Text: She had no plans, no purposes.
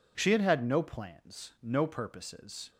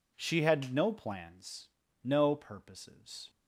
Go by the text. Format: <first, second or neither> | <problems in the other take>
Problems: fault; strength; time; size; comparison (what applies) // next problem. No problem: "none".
second | says "had" twice; at 0.4 s